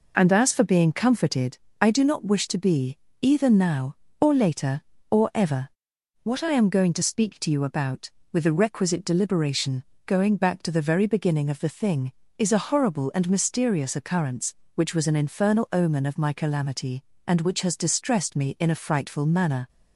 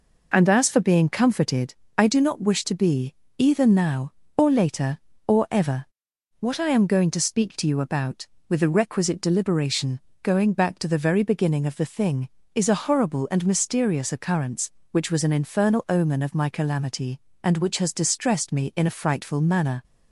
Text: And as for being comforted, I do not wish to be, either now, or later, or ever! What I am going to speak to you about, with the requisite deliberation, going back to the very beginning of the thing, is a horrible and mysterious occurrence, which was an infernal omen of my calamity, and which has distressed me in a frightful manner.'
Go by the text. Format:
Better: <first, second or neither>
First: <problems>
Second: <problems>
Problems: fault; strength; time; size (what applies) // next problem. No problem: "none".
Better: neither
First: none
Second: none